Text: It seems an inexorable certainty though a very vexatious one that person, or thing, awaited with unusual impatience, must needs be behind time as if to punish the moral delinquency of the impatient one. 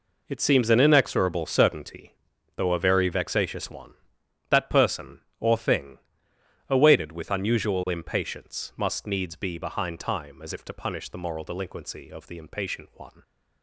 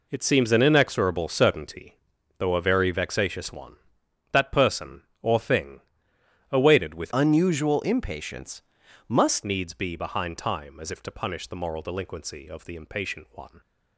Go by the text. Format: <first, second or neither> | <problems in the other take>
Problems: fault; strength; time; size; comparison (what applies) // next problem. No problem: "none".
first | pauses between "certainty" and "though"; noticeable; at 1.9 s; 0.46 s long; noticeable in the first // changes voice from "unusual" to "must"; from 7.1 to 9.4 s; 2.3 s long